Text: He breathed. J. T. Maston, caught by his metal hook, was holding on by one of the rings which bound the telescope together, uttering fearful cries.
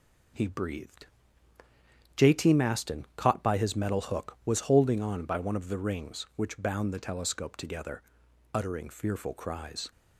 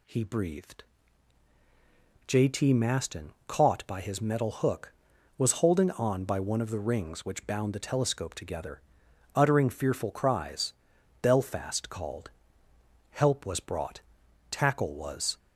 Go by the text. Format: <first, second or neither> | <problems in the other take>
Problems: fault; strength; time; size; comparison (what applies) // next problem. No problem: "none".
first | goes on to say "Belfast called Help was brought tackle was"; strong; from 11.2 s on; 4.1 s long